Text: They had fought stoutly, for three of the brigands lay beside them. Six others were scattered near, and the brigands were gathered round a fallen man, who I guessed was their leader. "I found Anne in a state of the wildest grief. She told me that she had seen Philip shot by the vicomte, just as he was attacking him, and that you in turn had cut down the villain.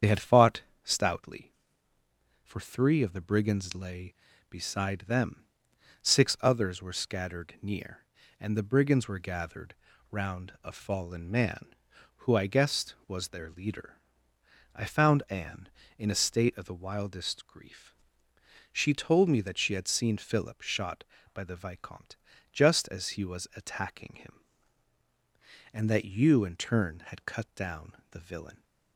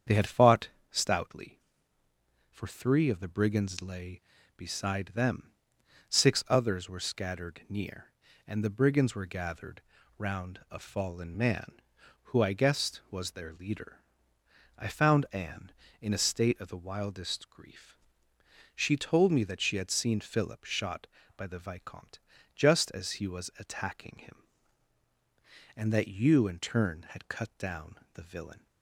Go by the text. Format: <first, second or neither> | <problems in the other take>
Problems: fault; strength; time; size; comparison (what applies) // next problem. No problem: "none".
second | loses the start of "They"; at 0.0 s; 25 ms // starts louder than the rest; strong; until 1.2 s; 8 dB; strong in the second // pauses between "fought" and "stoutly"; slight; at 0.6 s; 0.20 s long; slight in the second // pauses between "gathered" and "round"; slight; at 9.7 s; 0.36 s long; slight in the second